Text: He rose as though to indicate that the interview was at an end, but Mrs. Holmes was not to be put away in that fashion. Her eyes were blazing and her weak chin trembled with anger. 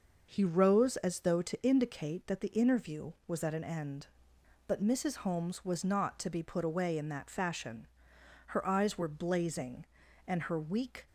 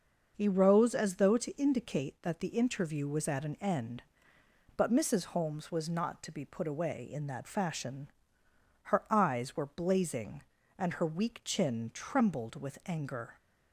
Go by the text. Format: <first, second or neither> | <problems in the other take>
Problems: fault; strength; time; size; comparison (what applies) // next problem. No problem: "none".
second | stops before "chin trembled with anger"; at 11.0 s